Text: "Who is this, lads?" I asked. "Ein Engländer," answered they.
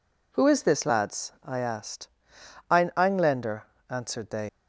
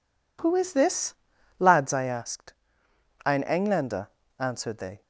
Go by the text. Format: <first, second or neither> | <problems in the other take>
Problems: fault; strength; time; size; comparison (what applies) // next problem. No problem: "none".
second | leaves "they" unfinished; at 4.4 s; 110 ms